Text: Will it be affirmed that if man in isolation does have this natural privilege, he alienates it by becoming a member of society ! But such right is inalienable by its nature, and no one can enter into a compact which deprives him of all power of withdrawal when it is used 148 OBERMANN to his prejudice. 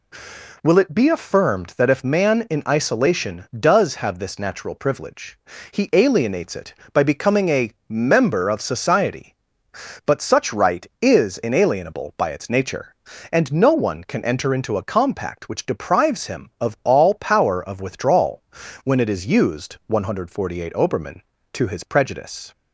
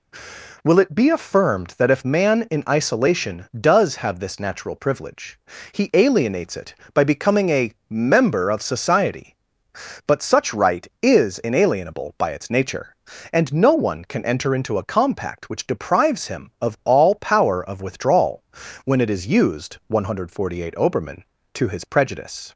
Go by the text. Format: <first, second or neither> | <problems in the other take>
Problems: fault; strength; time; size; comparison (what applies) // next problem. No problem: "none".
neither | pauses between "a" and "member"; slight; the same in both // pauses between "withdrawal" and "when"; the same in both